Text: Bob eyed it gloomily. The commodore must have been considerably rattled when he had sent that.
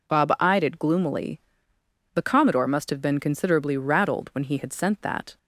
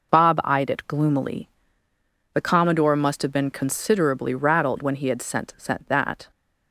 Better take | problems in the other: first | says "sent" twice; at 5.5 s

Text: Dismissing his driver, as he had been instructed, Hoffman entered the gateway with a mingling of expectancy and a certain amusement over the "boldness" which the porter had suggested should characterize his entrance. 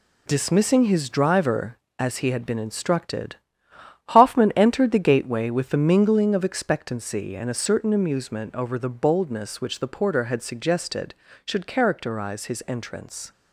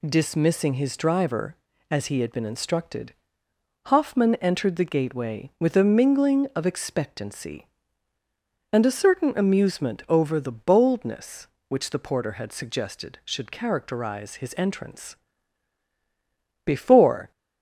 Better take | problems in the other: first | goes on to say "Before"; noticeable; from 16.6 s on; 0.66 s long

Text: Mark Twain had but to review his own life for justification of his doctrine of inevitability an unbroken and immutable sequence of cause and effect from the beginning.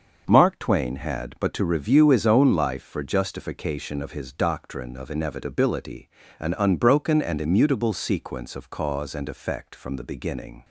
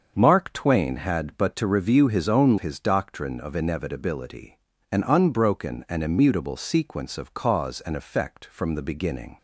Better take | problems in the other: first | starts louder than the rest; until 1.1 s; 6.5 dB; also in the first // skips "life for justification of"; at 2.5 s // pauses between "inevitability" and "an"; slight; at 4.5 s; 0.32 s long; slight in the first

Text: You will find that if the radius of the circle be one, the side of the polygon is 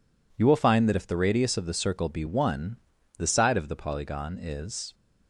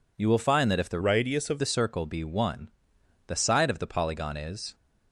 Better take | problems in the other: first | changes voice from "radius" to "of"; from 1.0 to 1.6 s; 0.6 s long

